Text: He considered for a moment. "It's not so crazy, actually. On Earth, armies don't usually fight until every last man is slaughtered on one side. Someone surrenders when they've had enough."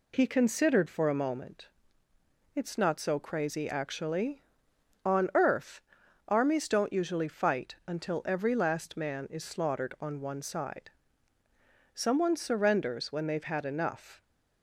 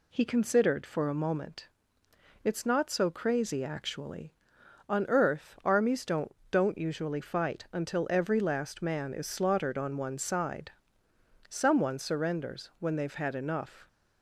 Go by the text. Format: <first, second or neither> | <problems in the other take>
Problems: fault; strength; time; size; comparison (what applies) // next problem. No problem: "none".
first | says "don't" twice; at 6.5 s